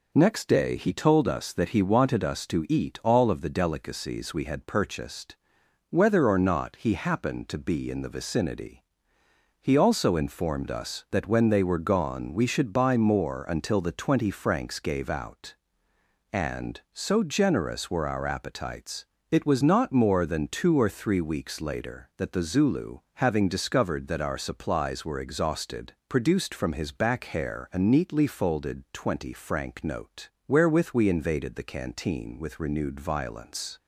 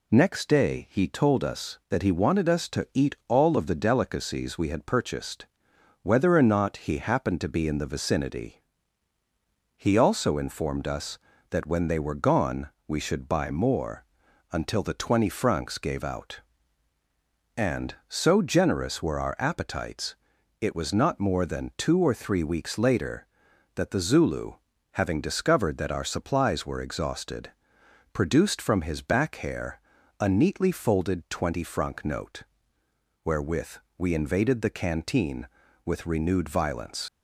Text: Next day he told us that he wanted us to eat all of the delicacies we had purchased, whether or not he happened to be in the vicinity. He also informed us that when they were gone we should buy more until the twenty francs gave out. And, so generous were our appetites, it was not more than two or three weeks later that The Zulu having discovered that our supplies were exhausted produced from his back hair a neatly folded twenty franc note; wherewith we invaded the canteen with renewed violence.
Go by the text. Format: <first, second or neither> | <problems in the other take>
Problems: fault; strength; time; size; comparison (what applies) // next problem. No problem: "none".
first | pauses between "gone" and "we"; slight; at 12.6 s; 0.18 s long // pauses between "more" and "until"; noticeable; at 14.0 s; 0.48 s long // pauses between "Zulu" and "having"; at 24.5 s; 0.38 s long; slight in the first // pauses between "exhausted" and "produced"; noticeable; at 27.5 s; 0.60 s long; slight in the first // pauses between "hair" and "a"; at 29.7 s; 0.40 s long // pauses between "wherewith" and "we"; slight; at 33.7 s; 0.22 s long // leaves "violence" unfinished; at 37.0 s; 45 ms